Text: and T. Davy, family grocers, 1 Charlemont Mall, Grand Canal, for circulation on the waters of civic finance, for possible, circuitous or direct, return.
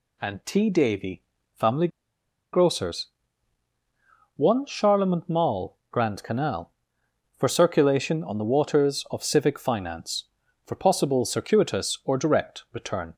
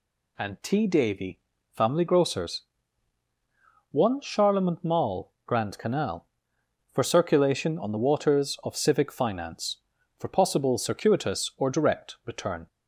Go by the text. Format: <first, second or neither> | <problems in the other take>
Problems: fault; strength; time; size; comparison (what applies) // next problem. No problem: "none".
second | pauses between "family" and "grocers"; noticeable; at 1.8 s; 0.64 s long